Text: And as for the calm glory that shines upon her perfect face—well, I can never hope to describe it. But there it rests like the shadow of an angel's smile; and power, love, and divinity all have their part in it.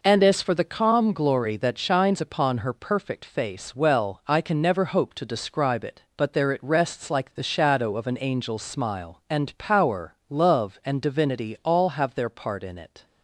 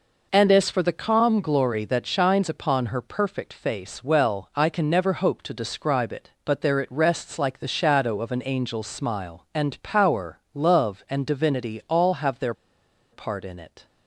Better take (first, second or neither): first